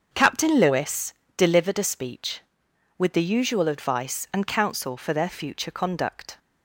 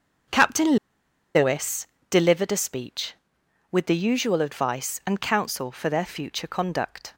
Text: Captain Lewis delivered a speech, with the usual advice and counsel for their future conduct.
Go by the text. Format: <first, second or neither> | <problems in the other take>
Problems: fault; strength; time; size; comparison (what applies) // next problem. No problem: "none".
first | starts louder than the rest; until 2.1 s; 6.5 dB; also in the first // pauses between "Captain" and "Lewis"; noticeable; at 0.7 s; 0.59 s long // pauses between "Lewis" and "delivered"; slight; at 1.8 s; 0.24 s long; slight in the first